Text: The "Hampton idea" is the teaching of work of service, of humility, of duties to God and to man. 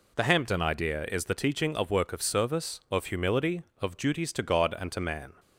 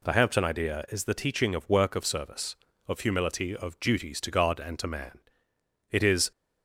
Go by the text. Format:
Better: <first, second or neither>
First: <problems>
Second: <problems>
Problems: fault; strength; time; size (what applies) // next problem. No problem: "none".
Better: first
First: none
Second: goes on to say "It is"; slight; from 5.9 s on; 0.40 s long